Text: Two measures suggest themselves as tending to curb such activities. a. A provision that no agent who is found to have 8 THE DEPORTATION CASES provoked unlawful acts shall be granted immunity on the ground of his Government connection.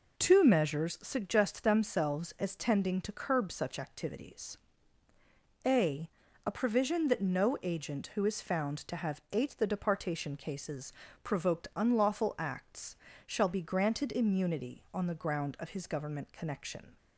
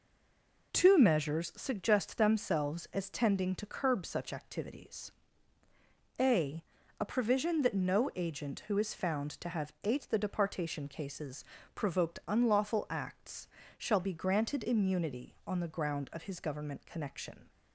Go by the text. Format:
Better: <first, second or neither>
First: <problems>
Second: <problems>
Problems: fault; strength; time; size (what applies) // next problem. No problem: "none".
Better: first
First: pauses between "CASES" and "provoked"; slight; at 10.9 s; 0.32 s long // pauses between "acts" and "shall"; slight; at 12.9 s; 0.30 s long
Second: stays silent before the first word; slight; until 0.7 s; 0.7 s long // pauses between "CASES" and "provoked"; slight; at 11.4 s; 0.32 s long // pauses between "acts" and "shall"; slight; at 13.4 s; 0.30 s long